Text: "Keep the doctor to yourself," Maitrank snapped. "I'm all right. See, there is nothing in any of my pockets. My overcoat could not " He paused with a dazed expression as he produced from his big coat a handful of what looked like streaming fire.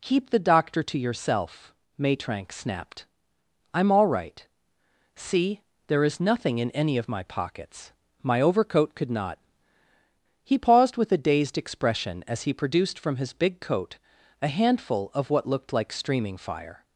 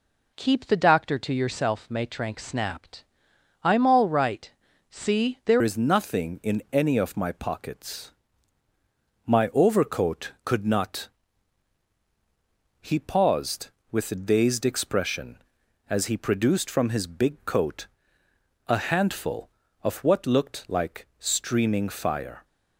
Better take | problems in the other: first | changes voice at "is"; from 5.6 s on; 16.8 s long // pauses between "coat" and "a"; noticeable; at 17.8 s; 0.80 s long; also in the first

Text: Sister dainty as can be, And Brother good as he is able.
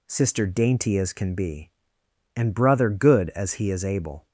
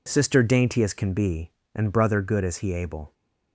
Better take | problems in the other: first | skips "is"; at 2.7 s

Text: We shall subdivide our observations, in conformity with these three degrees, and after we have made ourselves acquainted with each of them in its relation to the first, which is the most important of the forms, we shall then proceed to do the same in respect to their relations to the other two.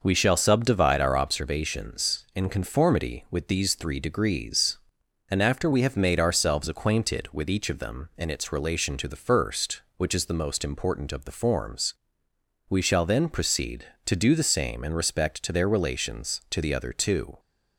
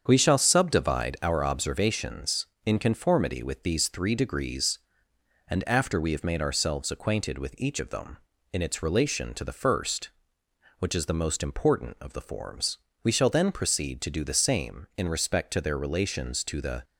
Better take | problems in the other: first | starts louder than the rest; strong; until 1.0 s; 7.5 dB // stops before "other two"; at 16.8 s

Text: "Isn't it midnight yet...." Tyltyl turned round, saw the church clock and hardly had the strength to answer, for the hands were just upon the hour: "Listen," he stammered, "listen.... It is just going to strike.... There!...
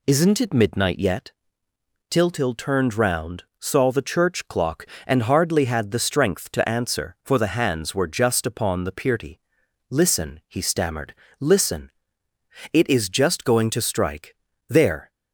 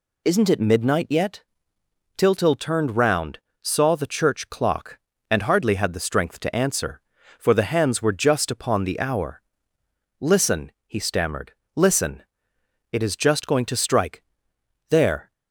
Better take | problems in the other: second | says "pirty" for "hour"; at 8.9 s

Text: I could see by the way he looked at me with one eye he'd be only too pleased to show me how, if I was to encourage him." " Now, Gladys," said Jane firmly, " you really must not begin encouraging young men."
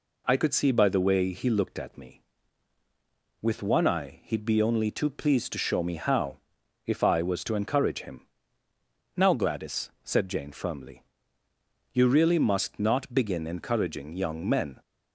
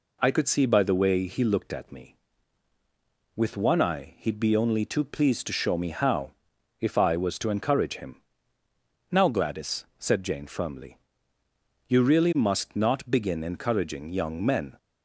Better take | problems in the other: neither | none

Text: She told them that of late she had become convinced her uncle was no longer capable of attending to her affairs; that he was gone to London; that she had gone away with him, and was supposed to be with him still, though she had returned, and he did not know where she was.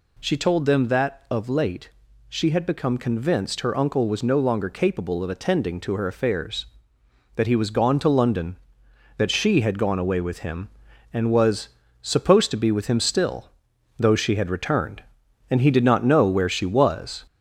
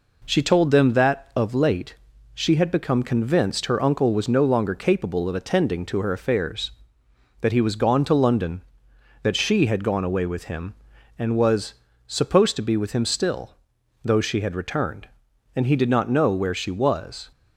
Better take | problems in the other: second | gets louder; throughout; 3.5 dB // pauses between "late" and "she"; at 1.8 s; 0.38 s long; also in the second // pauses between "was" and "supposed"; slight; at 11.6 s; 0.34 s long; slight in the second

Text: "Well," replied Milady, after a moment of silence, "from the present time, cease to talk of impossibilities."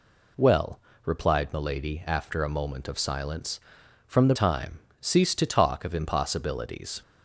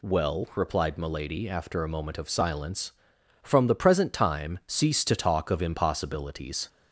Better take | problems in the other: second | skips "present"; at 4.3 s

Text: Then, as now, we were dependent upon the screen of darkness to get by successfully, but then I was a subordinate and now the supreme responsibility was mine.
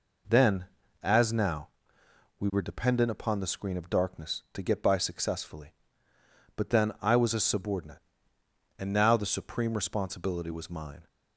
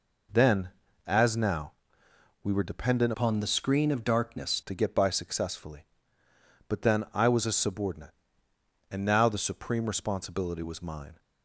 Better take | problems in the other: first | changes voice from "upon" to "darkness"; from 3.1 to 4.6 s; 1.5 s long

